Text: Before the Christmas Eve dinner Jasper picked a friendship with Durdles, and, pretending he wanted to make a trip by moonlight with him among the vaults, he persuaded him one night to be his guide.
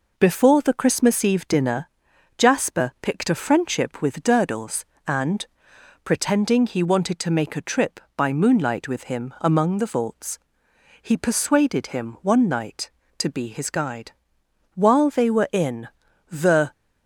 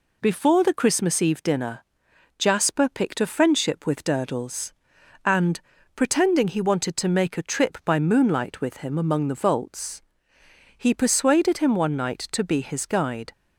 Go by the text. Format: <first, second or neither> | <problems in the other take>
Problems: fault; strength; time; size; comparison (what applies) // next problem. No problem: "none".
second | pauses between "dinner" and "Jasper"; noticeable; at 1.8 s; 0.50 s long; noticeable in the second // goes on to say "While they were in the"; strong; from 14.7 s on; 1.9 s long